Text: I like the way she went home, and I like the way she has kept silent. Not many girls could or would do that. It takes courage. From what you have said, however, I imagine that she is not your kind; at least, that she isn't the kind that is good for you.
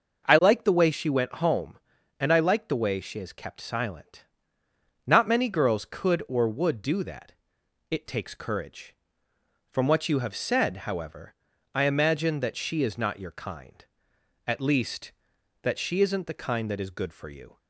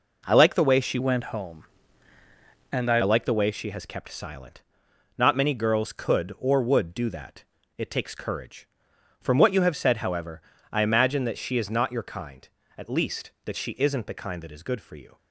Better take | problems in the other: first | changes voice from "went" to "I"; from 0.9 to 2.9 s; 2.0 s long

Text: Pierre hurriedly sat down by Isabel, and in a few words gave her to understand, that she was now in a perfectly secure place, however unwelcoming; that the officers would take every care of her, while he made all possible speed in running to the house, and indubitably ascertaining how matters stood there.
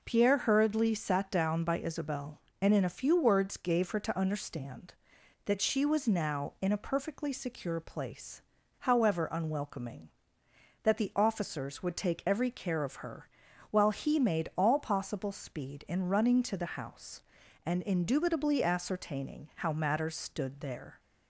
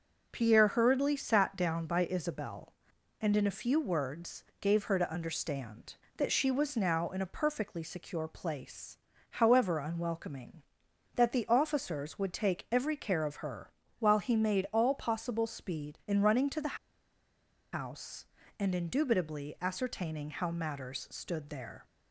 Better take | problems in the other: first | pauses between "words" and "gave"; slight; at 4.4 s; 0.16 s long // pauses between "the" and "house"; noticeable; at 16.7 s; 0.96 s long

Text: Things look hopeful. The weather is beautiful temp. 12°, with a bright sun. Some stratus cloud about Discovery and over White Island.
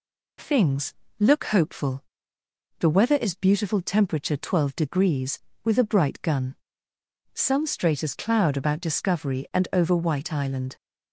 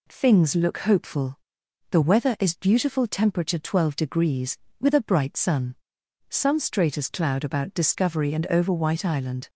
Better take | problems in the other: second | pauses between "Things" and "look"; slight; at 0.9 s; 0.26 s long // says "gun" for "sun"; at 6.2 s

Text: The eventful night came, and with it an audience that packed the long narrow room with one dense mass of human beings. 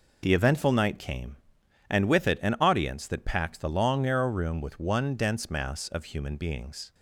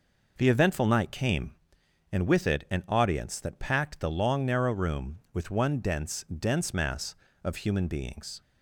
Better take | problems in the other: first | says "dense" twice; at 6.3 s

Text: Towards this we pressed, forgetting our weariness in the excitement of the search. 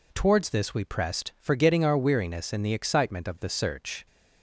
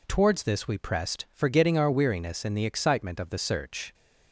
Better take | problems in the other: neither | none

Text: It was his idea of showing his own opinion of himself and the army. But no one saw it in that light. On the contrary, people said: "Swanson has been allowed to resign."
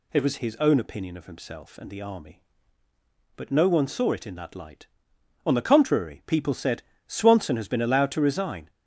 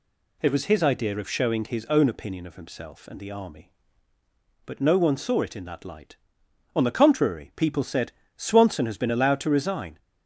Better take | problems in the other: second | skips "his idea of showing"; at 0.3 s

